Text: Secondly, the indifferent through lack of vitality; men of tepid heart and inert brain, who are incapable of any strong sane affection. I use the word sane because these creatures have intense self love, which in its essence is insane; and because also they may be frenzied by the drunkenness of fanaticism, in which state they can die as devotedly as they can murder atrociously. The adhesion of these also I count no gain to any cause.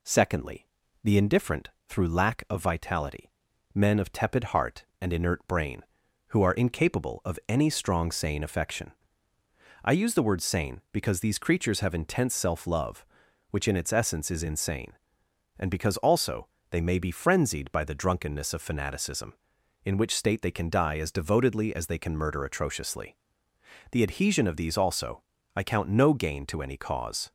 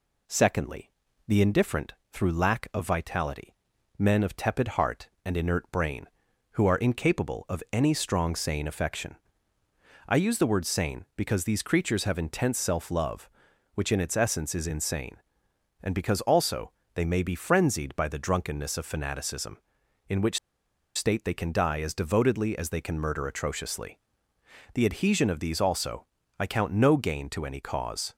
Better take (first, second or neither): first